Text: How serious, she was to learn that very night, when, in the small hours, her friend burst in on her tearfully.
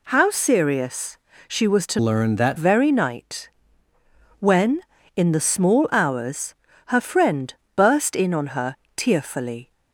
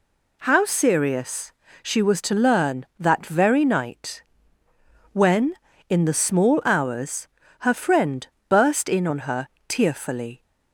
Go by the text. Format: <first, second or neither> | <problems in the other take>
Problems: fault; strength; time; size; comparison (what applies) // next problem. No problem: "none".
second | changes voice from "learn" to "that"; from 1.9 to 2.5 s; 0.6 s long // pauses between "friend" and "burst"; slight; at 7.5 s; 0.24 s long; slight in the second // pauses between "her" and "tearfully"; slight; at 8.7 s; 0.20 s long; slight in the second